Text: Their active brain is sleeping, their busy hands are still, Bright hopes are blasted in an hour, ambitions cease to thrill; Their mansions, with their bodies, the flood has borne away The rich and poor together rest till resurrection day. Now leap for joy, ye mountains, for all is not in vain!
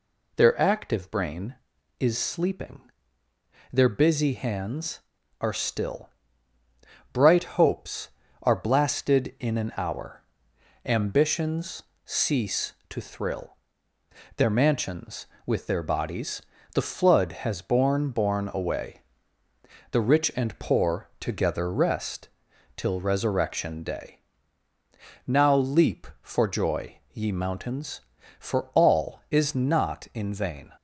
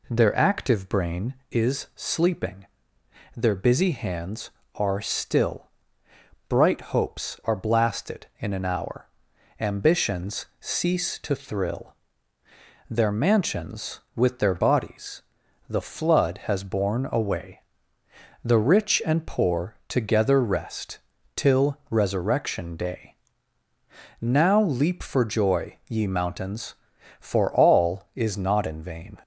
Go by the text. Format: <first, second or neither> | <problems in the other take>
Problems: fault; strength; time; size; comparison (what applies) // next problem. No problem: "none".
second | pauses between "ambitions" and "cease"; slight; at 11.8 s; 0.20 s long // says "borne" twice; at 18.0 s // pauses between "away" and "The"; noticeable; at 19.0 s; 0.90 s long; noticeable in the second // pauses between "rest" and "till"; noticeable; at 22.2 s; 0.48 s long; also in the second